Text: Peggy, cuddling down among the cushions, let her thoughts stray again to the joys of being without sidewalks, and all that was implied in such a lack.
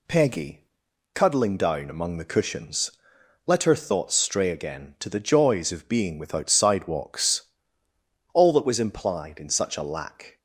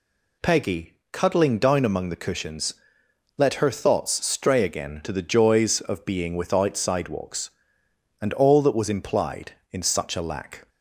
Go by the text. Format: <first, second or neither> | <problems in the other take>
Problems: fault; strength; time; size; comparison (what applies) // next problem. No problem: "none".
second | skips "and"; at 7.8 s